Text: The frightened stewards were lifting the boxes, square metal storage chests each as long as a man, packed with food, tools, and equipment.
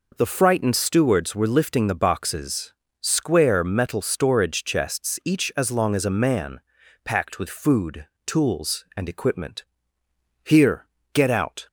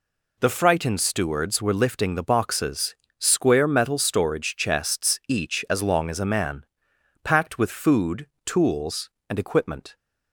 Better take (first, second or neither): second